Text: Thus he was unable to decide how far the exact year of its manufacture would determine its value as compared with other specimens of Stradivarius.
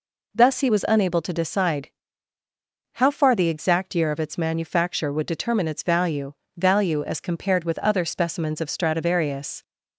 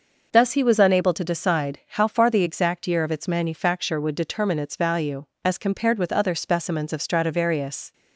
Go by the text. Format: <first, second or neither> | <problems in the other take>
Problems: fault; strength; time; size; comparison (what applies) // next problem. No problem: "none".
second | pauses between "decide" and "how"; at 1.8 s; 1.0 s long // says "value" twice; at 6.5 s